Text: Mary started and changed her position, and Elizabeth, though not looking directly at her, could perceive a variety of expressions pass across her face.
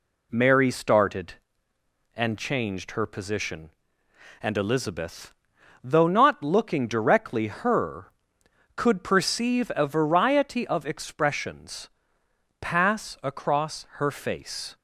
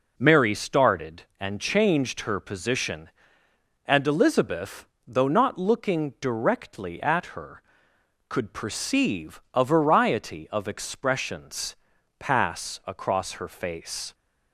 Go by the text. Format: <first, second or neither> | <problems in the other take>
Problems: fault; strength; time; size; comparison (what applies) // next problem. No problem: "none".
second | skips "at"; at 7.4 s // pauses between "expressions" and "pass"; noticeable; at 11.8 s; 0.72 s long; also in the second